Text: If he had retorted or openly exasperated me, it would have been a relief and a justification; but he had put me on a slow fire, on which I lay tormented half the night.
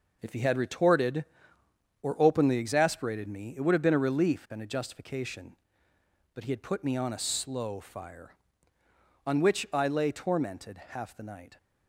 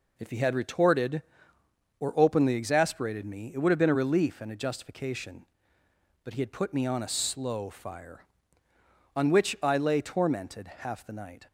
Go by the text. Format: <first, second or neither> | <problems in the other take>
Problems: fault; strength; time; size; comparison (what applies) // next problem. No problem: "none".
second | gets quieter; strong; throughout; 7.5 dB